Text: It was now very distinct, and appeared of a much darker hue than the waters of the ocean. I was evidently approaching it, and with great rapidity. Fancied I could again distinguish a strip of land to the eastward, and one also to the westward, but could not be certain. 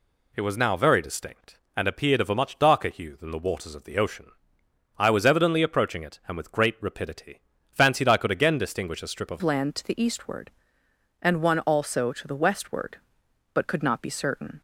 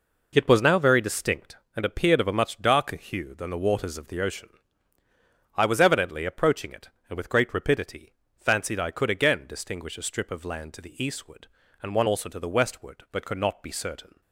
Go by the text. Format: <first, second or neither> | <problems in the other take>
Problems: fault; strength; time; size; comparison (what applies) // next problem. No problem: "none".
second | changes voice at "land"; from 9.4 s on; 5.2 s long